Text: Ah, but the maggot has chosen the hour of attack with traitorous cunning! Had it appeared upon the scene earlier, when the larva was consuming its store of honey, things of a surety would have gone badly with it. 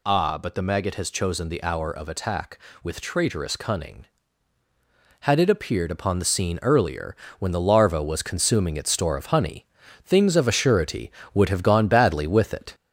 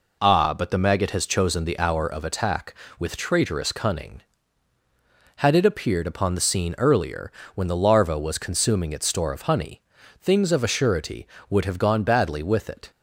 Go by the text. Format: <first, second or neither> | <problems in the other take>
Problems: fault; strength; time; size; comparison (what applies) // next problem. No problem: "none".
second | gets louder; slight; throughout; 3 dB